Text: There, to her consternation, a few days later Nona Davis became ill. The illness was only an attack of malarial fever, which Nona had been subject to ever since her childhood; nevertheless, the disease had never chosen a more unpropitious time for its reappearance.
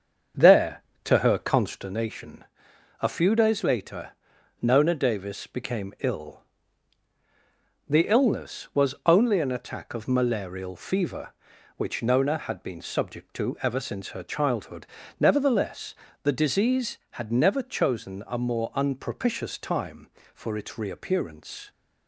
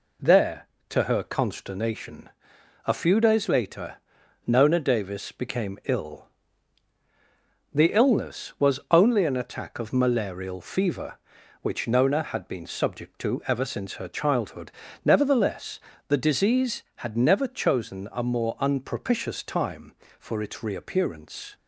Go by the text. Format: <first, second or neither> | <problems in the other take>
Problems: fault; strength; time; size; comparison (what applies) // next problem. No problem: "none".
second | starts louder than the rest; strong; until 1.9 s; 7 dB // pauses between "later" and "Nona"; noticeable; at 4.0 s; 0.50 s long; noticeable in the second